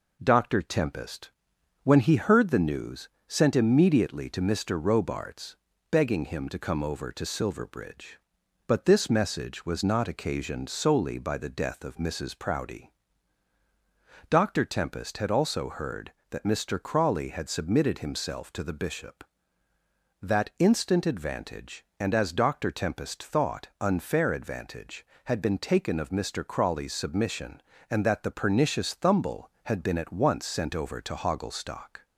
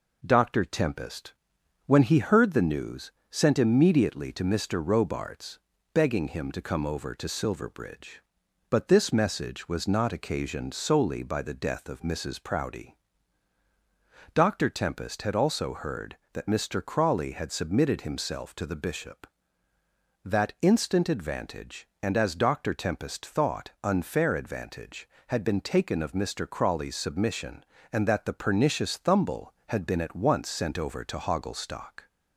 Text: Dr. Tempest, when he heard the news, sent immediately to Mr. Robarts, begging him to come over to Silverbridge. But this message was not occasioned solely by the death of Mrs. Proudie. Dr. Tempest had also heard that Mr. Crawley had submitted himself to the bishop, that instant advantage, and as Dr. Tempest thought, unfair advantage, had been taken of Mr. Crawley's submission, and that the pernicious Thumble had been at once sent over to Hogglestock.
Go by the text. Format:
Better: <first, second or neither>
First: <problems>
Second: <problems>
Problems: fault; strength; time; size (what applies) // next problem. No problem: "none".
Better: neither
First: none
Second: none